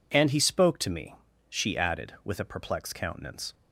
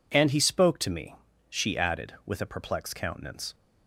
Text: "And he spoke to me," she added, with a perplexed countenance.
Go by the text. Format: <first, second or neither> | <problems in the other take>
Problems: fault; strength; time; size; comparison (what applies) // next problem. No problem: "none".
neither | none